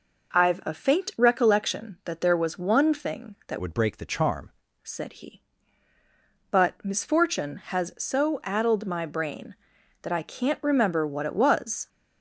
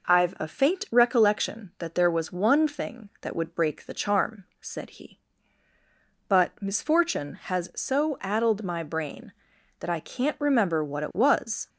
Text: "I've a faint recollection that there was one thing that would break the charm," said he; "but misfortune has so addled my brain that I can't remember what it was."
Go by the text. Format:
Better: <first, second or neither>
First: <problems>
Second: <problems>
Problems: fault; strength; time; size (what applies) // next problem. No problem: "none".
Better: second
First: changes voice from "would" to "charm"; from 3.6 to 4.5 s; 0.9 s long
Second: none